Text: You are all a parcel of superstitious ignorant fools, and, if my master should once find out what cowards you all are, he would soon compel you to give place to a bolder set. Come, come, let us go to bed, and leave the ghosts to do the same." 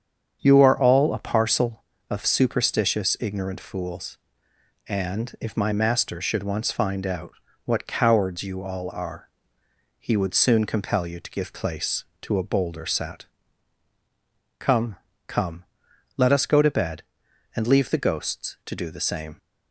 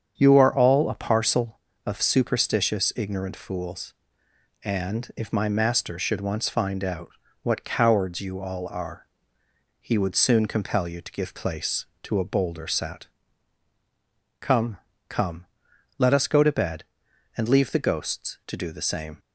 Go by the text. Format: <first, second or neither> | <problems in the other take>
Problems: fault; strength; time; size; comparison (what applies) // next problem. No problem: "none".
neither | starts louder than the rest; strong; the same in both // pauses between "out" and "what"; slight; the same in both